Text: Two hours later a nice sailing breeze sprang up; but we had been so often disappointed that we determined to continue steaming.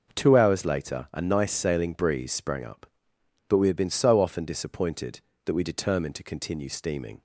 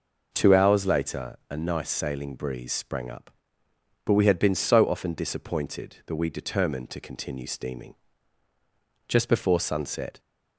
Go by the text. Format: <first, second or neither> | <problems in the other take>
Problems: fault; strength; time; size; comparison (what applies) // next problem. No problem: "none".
first | goes on to say "Just before sunset"; noticeable; from 9.0 s on; 1.1 s long